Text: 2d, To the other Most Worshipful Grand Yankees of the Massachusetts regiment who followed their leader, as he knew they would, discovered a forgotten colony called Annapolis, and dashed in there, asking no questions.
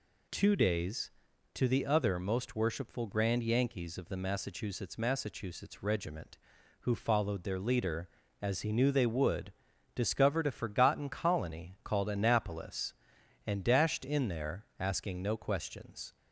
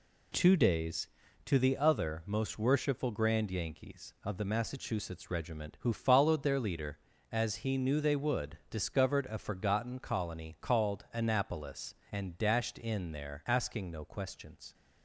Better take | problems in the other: second | says "Massachusetts" twice; at 4.9 s

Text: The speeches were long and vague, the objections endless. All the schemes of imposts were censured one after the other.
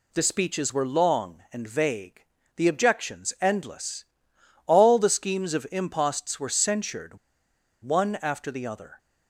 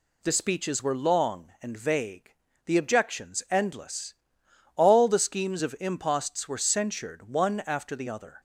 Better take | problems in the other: second | pauses between "censured" and "one"; noticeable; at 7.1 s; 0.65 s long

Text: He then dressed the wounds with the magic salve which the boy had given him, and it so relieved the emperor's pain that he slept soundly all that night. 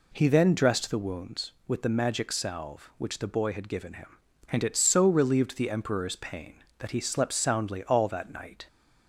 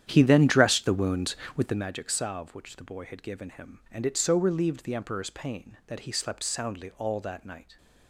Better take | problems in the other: first | starts louder than the rest; strong; until 1.9 s; 10 dB

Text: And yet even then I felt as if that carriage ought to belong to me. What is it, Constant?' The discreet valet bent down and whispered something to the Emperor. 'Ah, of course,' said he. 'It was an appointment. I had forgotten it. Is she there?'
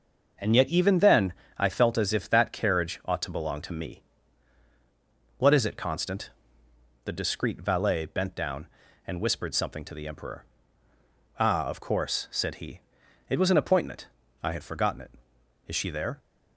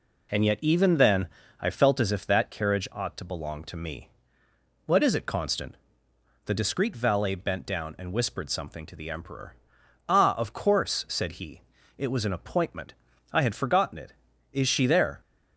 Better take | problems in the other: neither | pauses between "then" and "I"; slight; the same in both

